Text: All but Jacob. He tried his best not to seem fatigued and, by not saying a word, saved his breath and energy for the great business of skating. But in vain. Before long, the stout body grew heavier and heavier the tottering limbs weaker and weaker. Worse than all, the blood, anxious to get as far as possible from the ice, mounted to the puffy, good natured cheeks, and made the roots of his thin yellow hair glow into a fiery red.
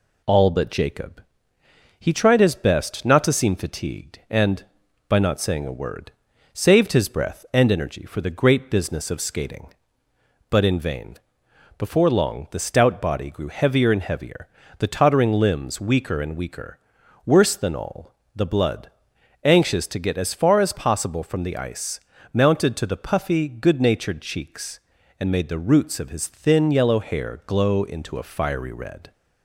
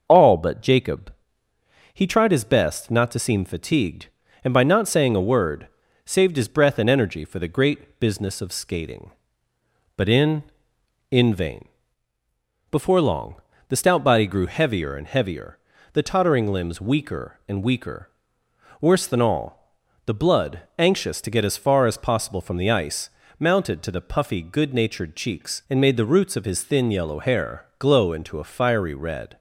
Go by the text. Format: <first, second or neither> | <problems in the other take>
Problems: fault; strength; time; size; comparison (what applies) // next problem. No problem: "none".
first | starts louder than the rest; until 1.0 s; 6 dB // says "in" twice; at 11.0 s // pauses between "heavier" and "the"; slight; at 15.5 s; 0.36 s long; slight in the first